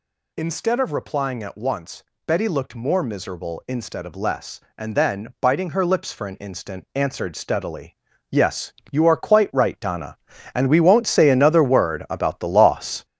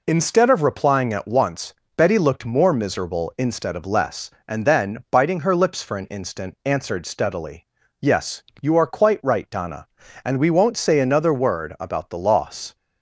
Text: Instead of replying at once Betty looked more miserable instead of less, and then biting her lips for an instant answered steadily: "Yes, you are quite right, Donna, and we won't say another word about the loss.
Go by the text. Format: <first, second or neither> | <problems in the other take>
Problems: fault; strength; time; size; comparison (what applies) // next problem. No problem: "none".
second | gets louder; throughout; 6.5 dB // pauses between "once" and "Betty"; slight; at 2.0 s; 0.22 s long; slight in the second